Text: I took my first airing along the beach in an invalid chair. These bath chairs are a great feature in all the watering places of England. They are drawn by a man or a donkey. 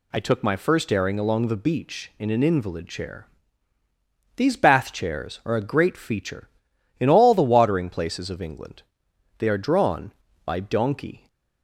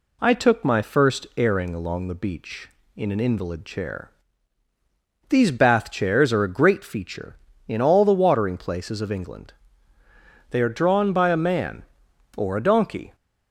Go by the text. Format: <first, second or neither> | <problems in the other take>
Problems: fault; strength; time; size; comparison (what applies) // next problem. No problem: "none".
second | skips "a man or a"; at 10.6 s